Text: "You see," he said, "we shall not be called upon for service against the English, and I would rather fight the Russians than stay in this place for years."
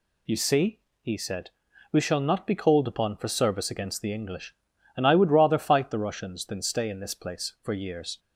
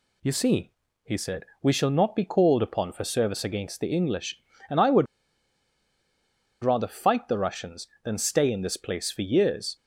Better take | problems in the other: first | pauses between "would" and "rather"; strong; at 5.0 s; 1.5 s long

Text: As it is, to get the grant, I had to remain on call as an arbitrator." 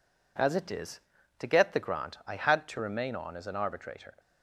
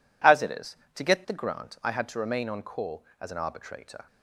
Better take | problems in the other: second | skips "call"; at 3.3 s

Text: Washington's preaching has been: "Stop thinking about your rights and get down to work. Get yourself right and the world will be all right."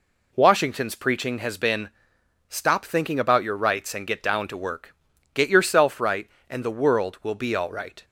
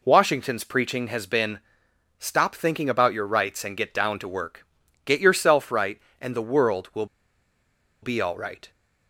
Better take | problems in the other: first | pauses between "will" and "be"; noticeable; at 7.0 s; 0.96 s long

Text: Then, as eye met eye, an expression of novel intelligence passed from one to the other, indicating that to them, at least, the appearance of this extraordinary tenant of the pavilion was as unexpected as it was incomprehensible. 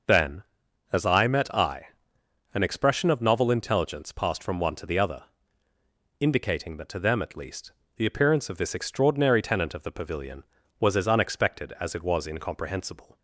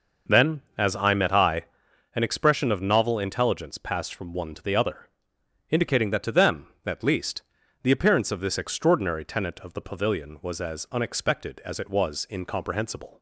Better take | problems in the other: neither | none

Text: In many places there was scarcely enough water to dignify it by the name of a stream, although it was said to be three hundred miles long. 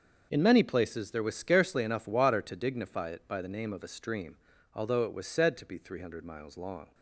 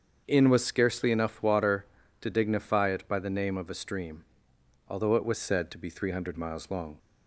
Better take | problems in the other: first | starts louder than the rest; until 1.2 s; 7 dB; also in the first // skips "many places there"; at 0.4 s

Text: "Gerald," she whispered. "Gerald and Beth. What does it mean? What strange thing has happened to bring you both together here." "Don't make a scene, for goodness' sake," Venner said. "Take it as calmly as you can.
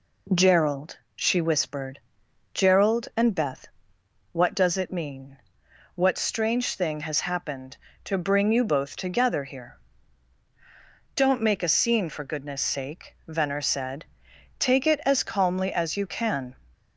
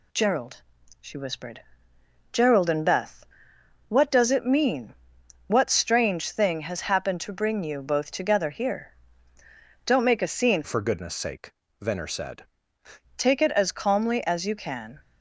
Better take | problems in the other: first | changes voice from "for" to "said"; from 10.6 to 12.4 s; 1.8 s long

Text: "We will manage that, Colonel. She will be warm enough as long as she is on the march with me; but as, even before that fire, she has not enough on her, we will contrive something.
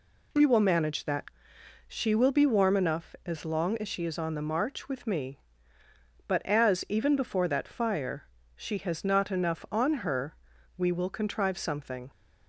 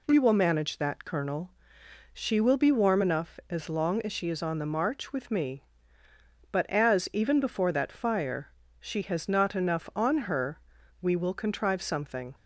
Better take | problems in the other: second | skips "Colonel"; at 1.5 s

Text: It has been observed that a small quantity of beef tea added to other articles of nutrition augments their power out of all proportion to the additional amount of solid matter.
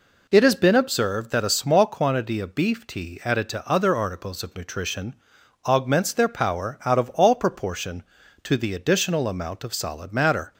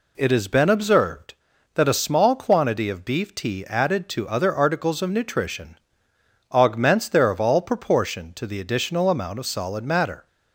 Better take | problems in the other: first | pauses between "nutrition" and "augments"; noticeable; at 5.7 s; 0.74 s long; noticeable in the first // skips "power out"; at 7.3 s

